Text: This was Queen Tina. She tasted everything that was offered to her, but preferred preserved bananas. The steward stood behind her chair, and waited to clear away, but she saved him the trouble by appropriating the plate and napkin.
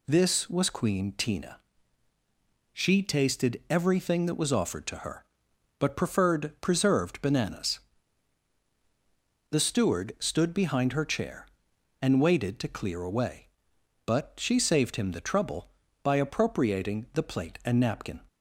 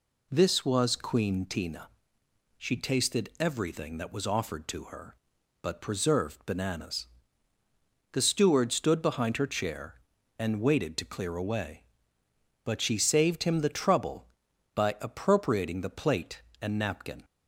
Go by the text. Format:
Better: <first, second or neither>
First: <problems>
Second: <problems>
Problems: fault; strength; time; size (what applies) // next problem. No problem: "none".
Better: first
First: none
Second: skips "preferred"; at 5.8 s